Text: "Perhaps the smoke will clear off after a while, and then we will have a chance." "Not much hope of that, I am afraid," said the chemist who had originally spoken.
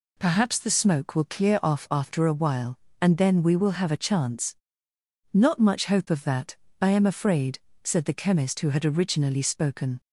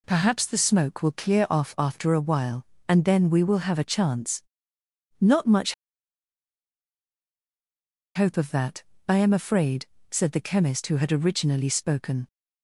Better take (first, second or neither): first